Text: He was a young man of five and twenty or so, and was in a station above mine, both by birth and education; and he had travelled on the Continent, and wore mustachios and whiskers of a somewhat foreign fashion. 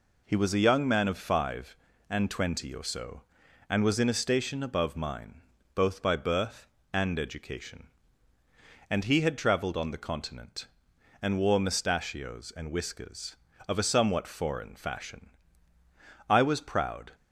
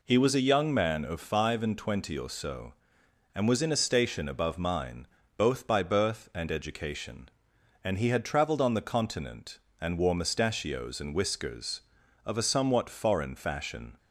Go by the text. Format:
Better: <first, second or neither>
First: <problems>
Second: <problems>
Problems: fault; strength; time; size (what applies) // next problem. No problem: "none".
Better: second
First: goes on to say "I was proud"; noticeable; from 16.2 s on; 0.82 s long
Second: none